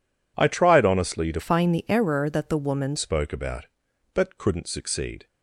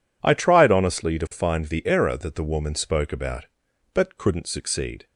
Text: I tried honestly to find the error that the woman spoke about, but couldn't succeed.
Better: second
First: changes voice from "find" to "woman"; from 1.3 to 2.9 s; 1.6 s long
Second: none

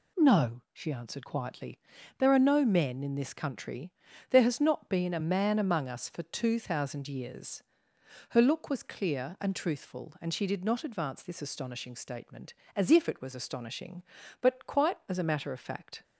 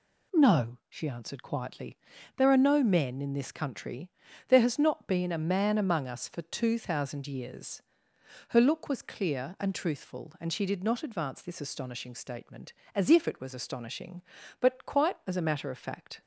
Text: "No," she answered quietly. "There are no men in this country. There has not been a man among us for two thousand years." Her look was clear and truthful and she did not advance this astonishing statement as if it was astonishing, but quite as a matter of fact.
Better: neither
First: none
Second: none

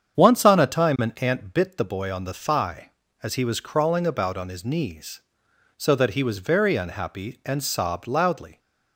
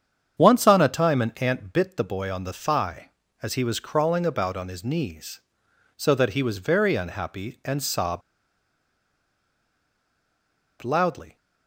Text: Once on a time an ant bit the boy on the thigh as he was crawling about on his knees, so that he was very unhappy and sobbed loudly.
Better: first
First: starts louder than the rest; strong; until 1.2 s; 8 dB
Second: starts louder than the rest; strong; until 1.4 s; 8 dB // pauses between "sobbed" and "loudly"; strong; at 8.2 s; 2.6 s long

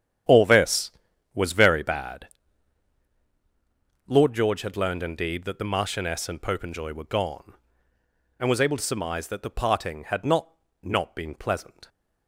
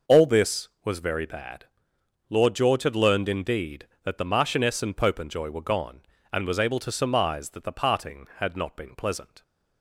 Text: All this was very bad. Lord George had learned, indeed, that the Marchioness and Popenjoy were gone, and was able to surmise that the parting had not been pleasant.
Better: second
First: starts louder than the rest; strong; until 1.7 s; 9.5 dB // says "not" twice; at 10.8 s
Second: none

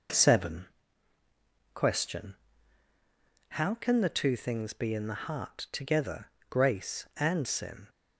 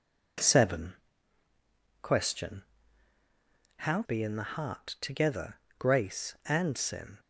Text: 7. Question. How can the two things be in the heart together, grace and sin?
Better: first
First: none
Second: skips "can the two things"; at 4.0 s

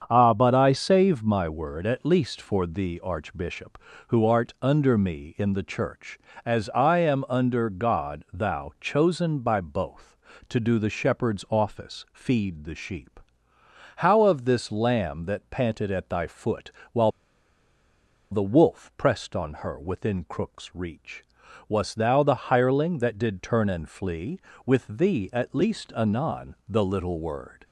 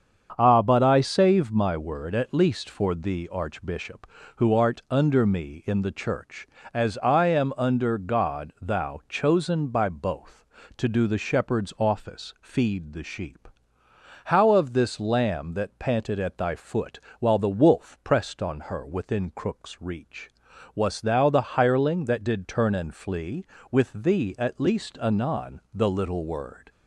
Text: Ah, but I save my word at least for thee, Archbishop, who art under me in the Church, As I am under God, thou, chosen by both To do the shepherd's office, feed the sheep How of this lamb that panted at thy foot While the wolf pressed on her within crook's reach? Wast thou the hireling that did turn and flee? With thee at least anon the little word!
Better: second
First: starts louder than the rest; strong; until 1.0 s; 7 dB // pauses between "sheep" and "How"; noticeable; at 13.2 s; 0.76 s long // pauses between "foot" and "While"; slight; at 16.7 s; 0.20 s long // pauses between "While" and "the"; at 17.1 s; 1.2 s long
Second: starts louder than the rest; strong; until 1.3 s; 7 dB // pauses between "sheep" and "How"; noticeable; at 13.4 s; 0.76 s long // pauses between "foot" and "While"; slight; at 16.9 s; 0.19 s long

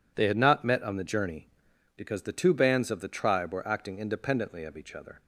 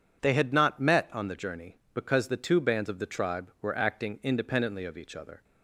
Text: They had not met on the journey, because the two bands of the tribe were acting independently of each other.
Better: neither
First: none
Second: none

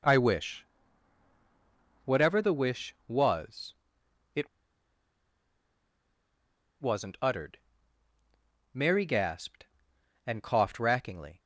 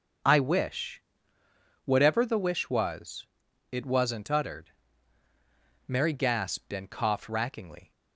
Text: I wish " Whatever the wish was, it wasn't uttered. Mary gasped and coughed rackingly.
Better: second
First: pauses between "it" and "wasn't"; strong; at 4.4 s; 2.3 s long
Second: none

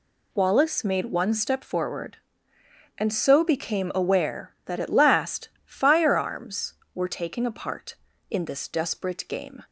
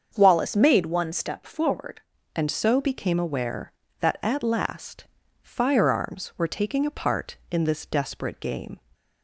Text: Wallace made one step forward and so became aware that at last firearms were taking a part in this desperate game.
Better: first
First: pauses between "last" and "firearms"; slight; at 5.4 s; 0.16 s long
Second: starts louder than the rest; until 1.2 s; 7 dB // changes voice at "and"; from 2.3 s on; 6.5 s long // pauses between "last" and "firearms"; slight; at 5.0 s; 0.36 s long

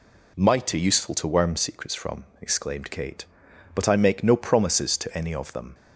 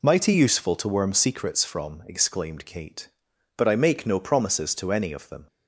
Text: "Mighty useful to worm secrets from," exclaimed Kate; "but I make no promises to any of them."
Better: neither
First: none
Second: none

